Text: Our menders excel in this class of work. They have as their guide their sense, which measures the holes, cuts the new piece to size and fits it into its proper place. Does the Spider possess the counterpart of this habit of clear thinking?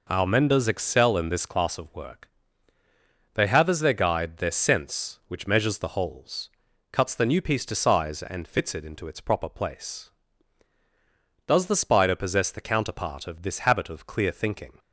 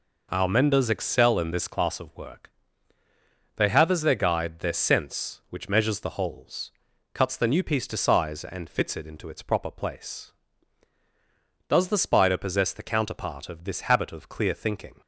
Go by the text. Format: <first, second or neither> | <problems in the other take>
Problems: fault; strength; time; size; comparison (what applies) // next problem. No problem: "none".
neither | none